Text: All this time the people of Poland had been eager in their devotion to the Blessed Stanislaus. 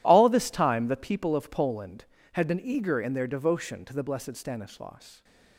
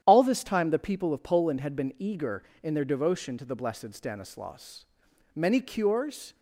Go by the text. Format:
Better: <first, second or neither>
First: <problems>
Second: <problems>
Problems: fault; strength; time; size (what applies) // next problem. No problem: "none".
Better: first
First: none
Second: starts louder than the rest; strong; until 1.0 s; 10.5 dB // goes on to say "Many cures"; noticeable; from 5.3 s on; 1.0 s long